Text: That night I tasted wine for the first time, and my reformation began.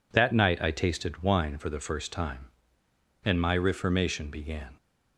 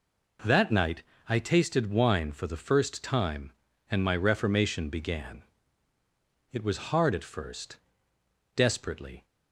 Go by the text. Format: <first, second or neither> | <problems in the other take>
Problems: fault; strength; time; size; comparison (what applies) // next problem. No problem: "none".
first | pauses between "night" and "I"; slight; at 1.0 s; 0.26 s long // goes on to say "It was hard at first desperately"; strong; from 6.5 s on; 2.7 s long